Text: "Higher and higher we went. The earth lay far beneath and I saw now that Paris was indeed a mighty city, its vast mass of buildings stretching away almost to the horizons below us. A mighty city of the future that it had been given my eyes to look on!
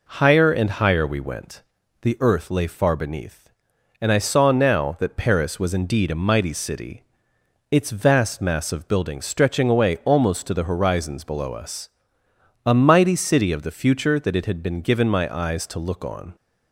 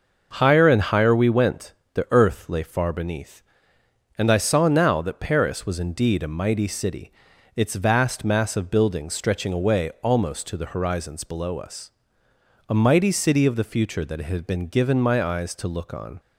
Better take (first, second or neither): neither